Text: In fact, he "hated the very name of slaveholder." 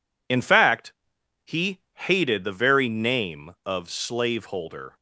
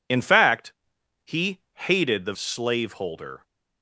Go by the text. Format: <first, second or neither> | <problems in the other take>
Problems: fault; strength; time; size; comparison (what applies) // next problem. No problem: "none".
first | pauses between "he" and "hated"; slight; at 1.5 s; 0.16 s long; slight in the first // skips "very name of"; at 2.3 s